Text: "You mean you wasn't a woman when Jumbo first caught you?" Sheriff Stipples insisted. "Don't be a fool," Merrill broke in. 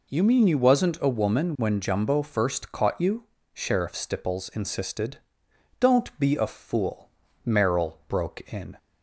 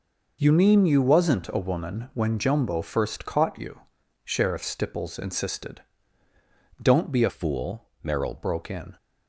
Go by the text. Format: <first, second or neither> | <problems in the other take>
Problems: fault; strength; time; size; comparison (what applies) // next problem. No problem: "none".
first | changes voice from "fool" to "Merrill"; from 7.2 to 8.3 s; 1.1 s long